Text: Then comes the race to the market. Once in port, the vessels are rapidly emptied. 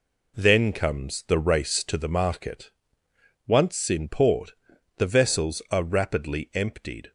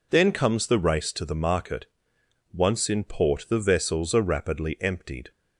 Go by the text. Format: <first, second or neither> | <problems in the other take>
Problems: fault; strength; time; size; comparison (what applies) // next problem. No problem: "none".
neither | none